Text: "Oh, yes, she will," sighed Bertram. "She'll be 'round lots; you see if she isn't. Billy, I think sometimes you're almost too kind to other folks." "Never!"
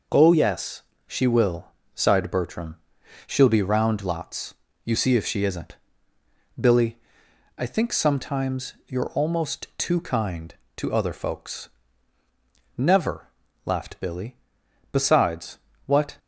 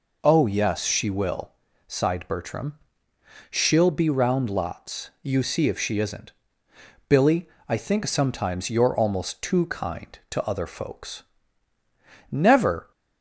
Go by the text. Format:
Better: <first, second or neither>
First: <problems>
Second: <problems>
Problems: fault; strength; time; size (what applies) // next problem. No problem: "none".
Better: second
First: goes on to say "laughed Billy Besides what"; strong; from 13.6 s on; 2.5 s long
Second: none